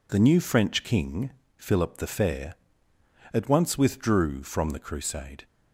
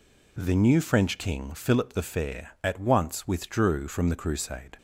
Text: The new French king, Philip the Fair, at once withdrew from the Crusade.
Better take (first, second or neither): neither